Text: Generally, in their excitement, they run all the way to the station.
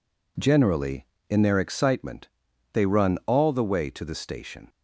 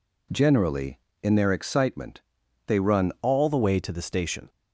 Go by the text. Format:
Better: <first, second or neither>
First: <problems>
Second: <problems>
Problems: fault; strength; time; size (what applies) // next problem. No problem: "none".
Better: first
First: none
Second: changes voice at "all"; from 3.2 s on; 1.2 s long